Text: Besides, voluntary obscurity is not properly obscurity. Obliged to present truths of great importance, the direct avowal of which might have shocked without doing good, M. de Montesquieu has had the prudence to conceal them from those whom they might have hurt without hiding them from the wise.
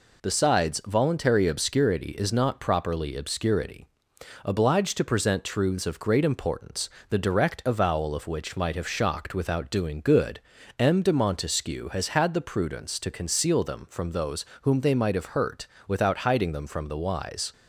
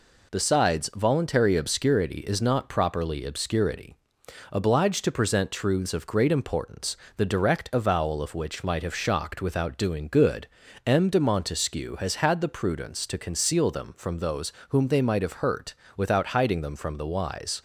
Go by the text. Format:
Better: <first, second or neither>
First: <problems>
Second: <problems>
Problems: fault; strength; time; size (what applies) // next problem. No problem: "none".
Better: neither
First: pauses between "those" and "whom"; slight; at 14.4 s; 0.18 s long // pauses between "hurt" and "without"; slight; at 15.6 s; 0.18 s long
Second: pauses between "those" and "whom"; slight; at 14.5 s; 0.18 s long // pauses between "hurt" and "without"; slight; at 15.7 s; 0.20 s long